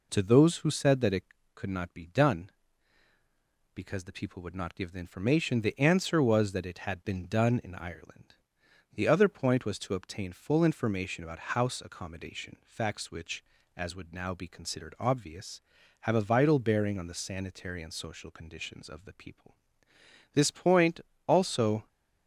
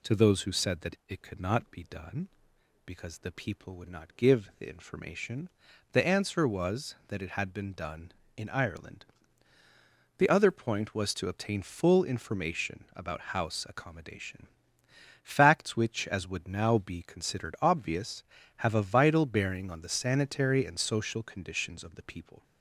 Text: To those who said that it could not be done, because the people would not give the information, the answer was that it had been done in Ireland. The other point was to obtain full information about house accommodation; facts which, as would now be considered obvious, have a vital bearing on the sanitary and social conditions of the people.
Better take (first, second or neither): second